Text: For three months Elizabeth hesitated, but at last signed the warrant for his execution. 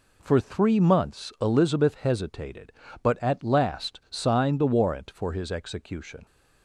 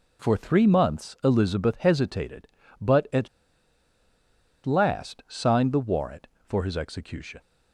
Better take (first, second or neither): first